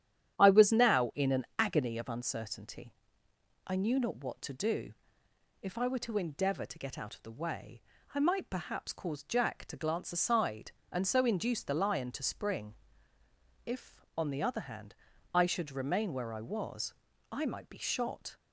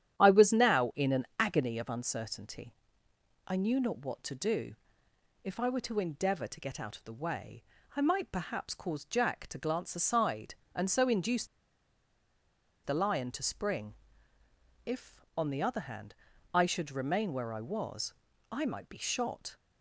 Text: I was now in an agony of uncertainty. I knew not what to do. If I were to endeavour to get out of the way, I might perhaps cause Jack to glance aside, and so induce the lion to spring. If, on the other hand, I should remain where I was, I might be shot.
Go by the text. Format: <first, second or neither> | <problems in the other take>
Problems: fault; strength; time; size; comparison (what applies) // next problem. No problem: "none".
first | starts louder than the rest; strong; until 1.2 s; 10.5 dB; strong in the first // pauses between "induce" and "the"; strong; at 11.4 s; 1.3 s long